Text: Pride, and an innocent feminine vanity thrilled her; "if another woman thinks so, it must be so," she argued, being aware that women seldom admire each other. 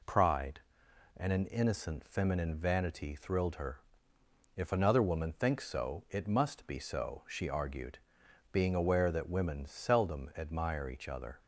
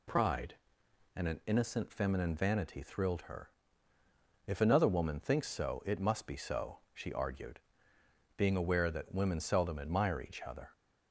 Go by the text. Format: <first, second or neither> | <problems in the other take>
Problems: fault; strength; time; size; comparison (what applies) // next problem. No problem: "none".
neither | none